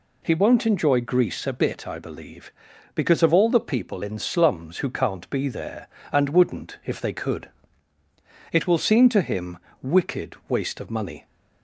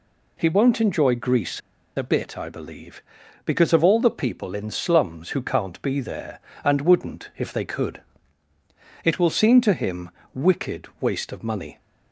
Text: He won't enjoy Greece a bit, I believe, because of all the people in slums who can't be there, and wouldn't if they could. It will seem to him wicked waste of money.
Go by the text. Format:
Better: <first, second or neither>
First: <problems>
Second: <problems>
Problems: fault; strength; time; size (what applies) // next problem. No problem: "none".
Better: first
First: pauses between "him" and "wicked"; slight; at 9.5 s; 0.24 s long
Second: pauses between "Greece" and "a"; at 1.5 s; 0.36 s long // pauses between "him" and "wicked"; slight; at 10.0 s; 0.24 s long